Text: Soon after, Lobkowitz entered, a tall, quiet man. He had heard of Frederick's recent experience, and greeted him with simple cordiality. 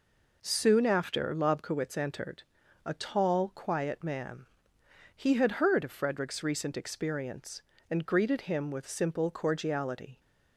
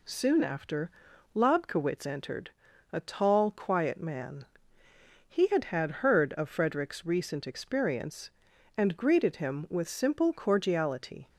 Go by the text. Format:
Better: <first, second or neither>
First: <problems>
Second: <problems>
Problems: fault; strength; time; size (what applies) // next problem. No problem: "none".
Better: first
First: none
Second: says "had" twice; at 5.6 s